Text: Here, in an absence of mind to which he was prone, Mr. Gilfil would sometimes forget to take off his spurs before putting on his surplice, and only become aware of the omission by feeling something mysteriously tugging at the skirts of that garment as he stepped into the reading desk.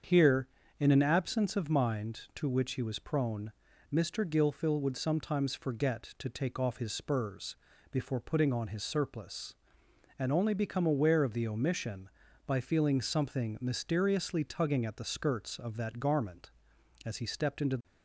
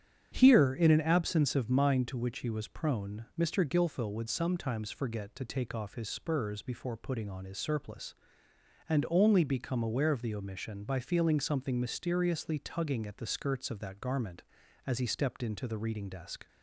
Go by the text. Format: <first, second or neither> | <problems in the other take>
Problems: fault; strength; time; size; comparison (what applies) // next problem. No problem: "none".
second | starts louder than the rest; strong; until 1.3 s; 7 dB; strong in the second // pauses between "spurs" and "before"; slight; at 7.5 s; 0.34 s long // stops before "reading desk"; at 17.8 s